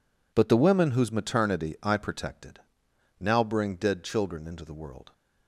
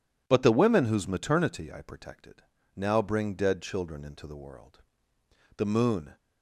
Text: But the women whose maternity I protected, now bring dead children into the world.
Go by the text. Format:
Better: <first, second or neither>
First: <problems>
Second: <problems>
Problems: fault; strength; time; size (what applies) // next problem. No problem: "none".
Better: first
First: none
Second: goes on to say "The moon"; from 5.5 s on; 0.60 s long